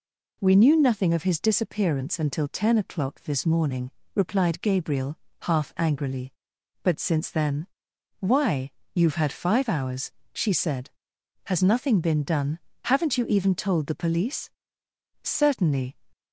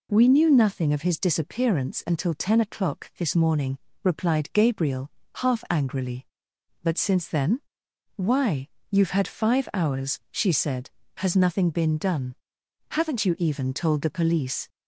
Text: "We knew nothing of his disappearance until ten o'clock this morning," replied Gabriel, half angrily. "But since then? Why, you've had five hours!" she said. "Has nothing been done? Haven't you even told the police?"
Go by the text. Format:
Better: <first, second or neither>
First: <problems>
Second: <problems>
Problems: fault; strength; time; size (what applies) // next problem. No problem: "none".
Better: second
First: goes on to say "Certainly"; noticeable; from 15.2 s on; 0.74 s long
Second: none